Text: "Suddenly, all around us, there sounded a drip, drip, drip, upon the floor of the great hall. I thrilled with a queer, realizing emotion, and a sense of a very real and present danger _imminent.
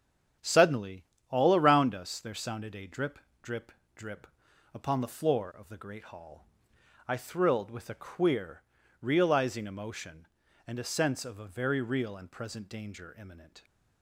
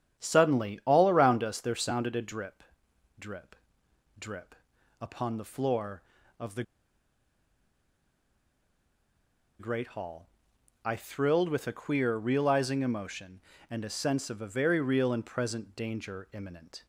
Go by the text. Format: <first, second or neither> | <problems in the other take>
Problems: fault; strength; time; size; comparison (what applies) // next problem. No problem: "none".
first | starts louder than the rest; strong; until 1.2 s; 9 dB; strong in the first // pauses between "the" and "great"; strong; at 6.6 s; 2.9 s long